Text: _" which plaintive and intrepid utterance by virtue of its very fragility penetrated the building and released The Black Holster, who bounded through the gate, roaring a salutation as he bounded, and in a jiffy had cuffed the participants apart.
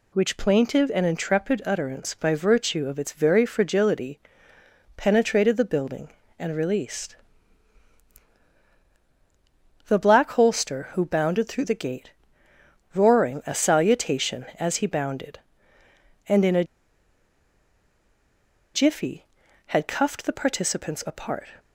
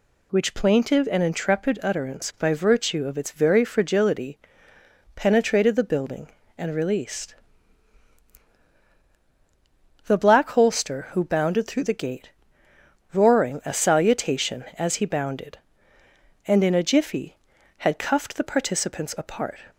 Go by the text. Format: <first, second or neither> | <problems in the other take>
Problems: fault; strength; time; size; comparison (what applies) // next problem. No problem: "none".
second | pauses between "fragility" and "penetrated"; noticeable; at 4.1 s; 0.76 s long; noticeable in the second // pauses between "released" and "The"; strong; at 7.1 s; 2.7 s long; strong in the second // pauses between "a" and "jiffy"; strong; at 16.6 s; 2.1 s long